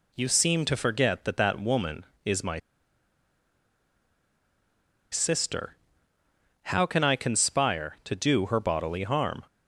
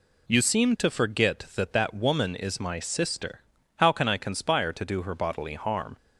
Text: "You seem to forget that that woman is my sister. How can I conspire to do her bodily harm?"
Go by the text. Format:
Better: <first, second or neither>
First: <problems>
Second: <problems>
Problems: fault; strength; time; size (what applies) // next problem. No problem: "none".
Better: second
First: pauses between "my" and "sister"; strong; at 2.5 s; 2.5 s long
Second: none